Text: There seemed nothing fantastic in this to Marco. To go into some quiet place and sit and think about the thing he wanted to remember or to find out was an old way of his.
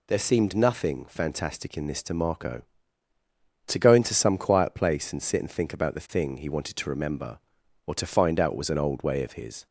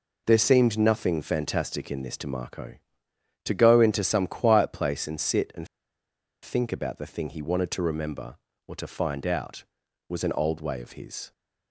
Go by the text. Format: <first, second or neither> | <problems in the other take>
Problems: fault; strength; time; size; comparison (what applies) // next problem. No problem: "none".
first | pauses between "and" and "think"; noticeable; at 5.6 s; 0.76 s long